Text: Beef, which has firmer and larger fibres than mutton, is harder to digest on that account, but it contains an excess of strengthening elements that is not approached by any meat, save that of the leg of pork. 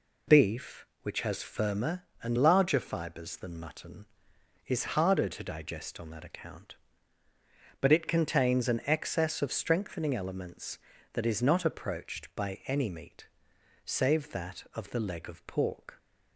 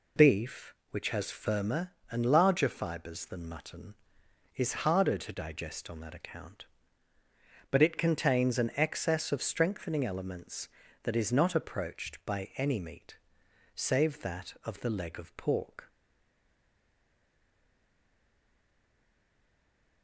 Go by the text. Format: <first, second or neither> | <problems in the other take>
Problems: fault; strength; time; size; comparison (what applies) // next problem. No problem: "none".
first | stays silent after the last word; strong; from 15.8 s on; 4.2 s long